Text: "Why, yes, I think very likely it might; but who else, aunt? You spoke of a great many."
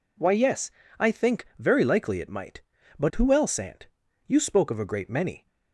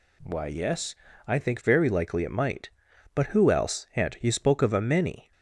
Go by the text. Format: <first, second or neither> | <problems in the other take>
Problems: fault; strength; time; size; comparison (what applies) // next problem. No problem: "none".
first | skips "great"; at 4.7 s